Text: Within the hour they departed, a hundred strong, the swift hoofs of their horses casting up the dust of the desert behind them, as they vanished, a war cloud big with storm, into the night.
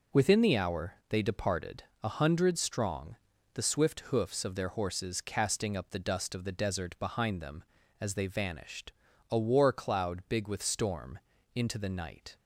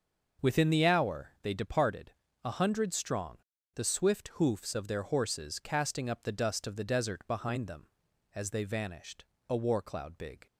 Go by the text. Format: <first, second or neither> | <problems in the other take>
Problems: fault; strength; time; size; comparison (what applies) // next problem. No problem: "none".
first | starts louder than the rest; until 1.5 s; 6.5 dB // stops before "with storm into the night"; at 10.4 s